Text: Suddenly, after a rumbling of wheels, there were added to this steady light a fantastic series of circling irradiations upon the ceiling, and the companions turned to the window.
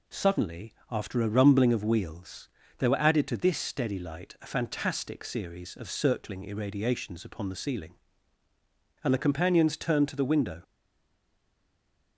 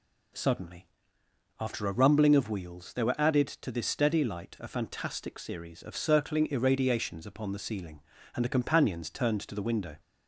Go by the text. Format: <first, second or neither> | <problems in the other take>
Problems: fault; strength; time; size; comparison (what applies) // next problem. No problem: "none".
second | stays silent after the last word; noticeable; from 10.6 s on; 1.5 s long